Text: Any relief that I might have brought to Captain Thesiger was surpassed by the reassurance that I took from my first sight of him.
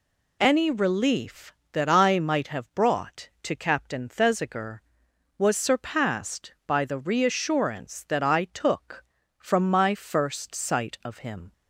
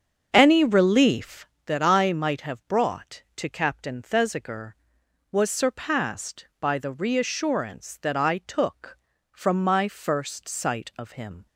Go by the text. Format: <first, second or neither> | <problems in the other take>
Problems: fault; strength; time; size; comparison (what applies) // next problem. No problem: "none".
first | starts louder than the rest; until 1.5 s; 7 dB